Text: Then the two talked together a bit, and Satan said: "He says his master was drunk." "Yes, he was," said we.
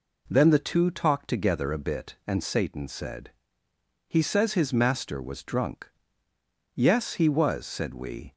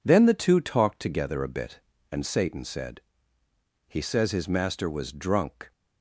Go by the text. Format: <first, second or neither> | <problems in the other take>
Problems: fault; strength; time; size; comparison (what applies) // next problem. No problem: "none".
first | stops before "Yes he was said we"; at 5.7 s